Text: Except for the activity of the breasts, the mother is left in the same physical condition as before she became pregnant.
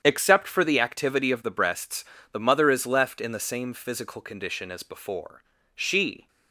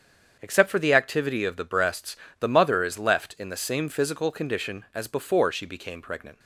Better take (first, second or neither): second